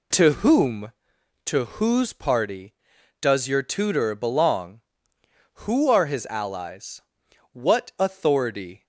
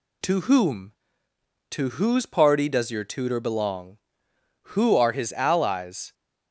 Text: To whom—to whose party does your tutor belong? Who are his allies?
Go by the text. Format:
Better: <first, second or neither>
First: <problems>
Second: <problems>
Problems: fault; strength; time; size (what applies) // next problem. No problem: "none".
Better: second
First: goes on to say "What authority"; noticeable; from 7.5 s on; 1.3 s long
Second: none